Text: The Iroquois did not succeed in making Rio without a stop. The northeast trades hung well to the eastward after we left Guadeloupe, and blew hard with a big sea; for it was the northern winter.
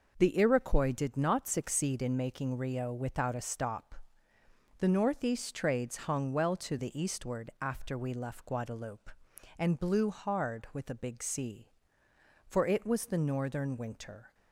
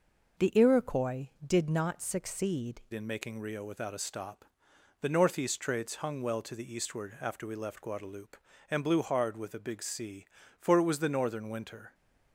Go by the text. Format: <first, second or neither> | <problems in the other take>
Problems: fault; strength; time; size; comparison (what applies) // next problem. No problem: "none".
first | changes voice at "in"; from 2.9 s on; 9.0 s long